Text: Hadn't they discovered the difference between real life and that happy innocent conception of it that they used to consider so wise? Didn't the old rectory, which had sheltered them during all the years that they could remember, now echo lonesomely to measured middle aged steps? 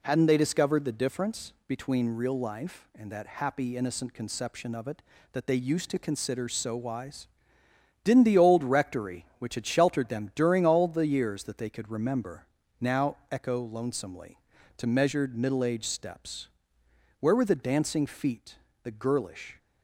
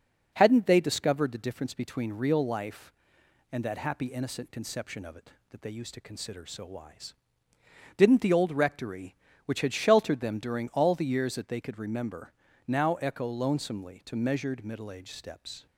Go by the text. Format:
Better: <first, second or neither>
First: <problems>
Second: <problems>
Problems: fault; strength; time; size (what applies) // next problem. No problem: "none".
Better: second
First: pauses between "difference" and "between"; slight; at 1.5 s; 0.16 s long // goes on to say "Where were the dancing feet the girlish"; strong; from 17.1 s on; 2.3 s long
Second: none